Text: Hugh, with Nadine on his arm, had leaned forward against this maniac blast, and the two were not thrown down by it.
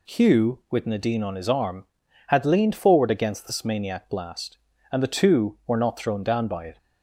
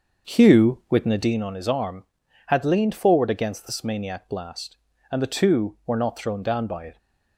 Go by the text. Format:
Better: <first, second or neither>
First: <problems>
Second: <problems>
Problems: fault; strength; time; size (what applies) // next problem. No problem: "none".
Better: first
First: none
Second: starts louder than the rest; until 1.4 s; 6.5 dB